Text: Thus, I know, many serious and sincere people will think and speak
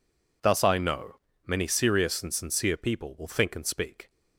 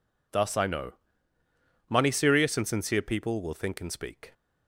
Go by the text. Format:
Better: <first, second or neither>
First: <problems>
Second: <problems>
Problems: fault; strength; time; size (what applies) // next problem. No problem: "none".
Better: first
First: none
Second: says "money" for "many"; at 1.8 s